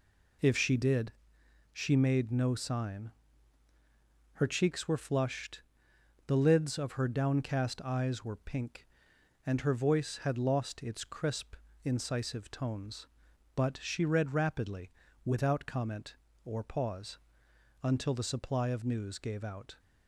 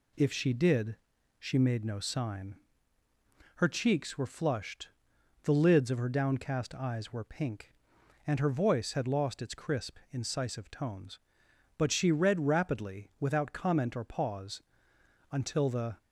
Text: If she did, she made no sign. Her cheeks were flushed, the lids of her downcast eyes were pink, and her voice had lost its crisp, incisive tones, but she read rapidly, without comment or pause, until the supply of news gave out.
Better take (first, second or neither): first